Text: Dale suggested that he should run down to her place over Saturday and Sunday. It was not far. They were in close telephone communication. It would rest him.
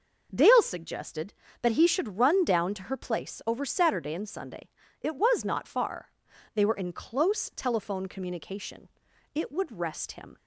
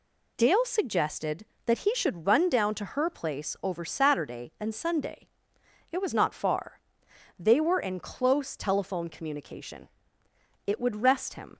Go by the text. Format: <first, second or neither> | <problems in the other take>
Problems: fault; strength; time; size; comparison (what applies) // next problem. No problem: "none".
neither | none